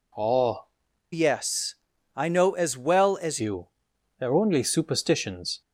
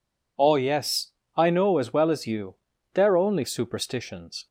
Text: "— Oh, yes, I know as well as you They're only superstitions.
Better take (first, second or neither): second